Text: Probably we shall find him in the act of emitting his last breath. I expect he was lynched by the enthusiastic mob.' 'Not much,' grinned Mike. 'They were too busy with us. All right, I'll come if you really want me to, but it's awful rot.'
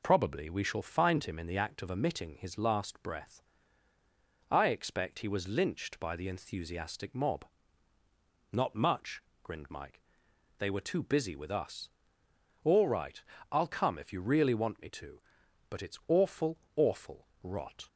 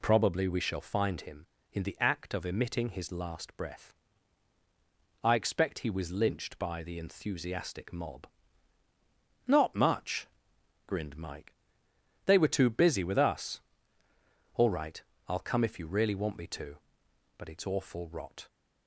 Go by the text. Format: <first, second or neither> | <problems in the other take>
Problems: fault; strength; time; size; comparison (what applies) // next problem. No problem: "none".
second | says "awful" twice; at 16.7 s